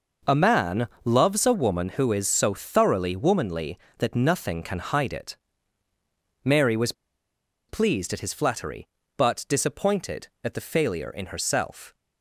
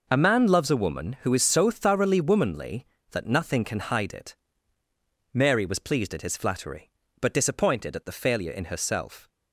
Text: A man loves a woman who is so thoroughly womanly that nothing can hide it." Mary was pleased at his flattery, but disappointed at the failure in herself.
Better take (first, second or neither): second